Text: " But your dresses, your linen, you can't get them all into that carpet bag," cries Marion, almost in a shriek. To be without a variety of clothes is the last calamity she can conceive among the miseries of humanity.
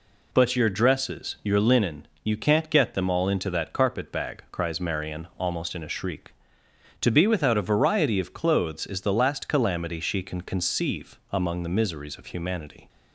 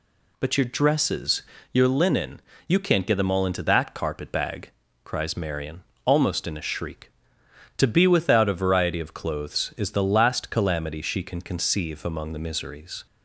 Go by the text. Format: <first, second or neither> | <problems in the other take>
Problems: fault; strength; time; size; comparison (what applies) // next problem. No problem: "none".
first | stops before "of humanity"; at 13.0 s